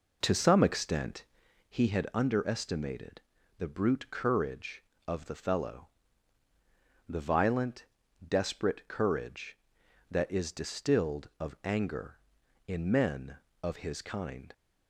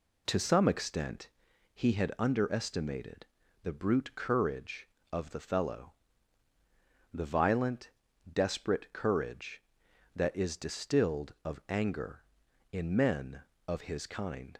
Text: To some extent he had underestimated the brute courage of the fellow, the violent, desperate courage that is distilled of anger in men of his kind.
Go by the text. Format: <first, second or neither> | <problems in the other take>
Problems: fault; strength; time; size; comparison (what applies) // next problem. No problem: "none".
second | starts louder than the rest; noticeable; until 1.7 s; 4.5 dB // pauses between "extent" and "he"; noticeable; at 1.2 s; 0.48 s long; noticeable in the second // pauses between "underestimated" and "the"; slight; at 3.2 s; 0.34 s long; slight in the second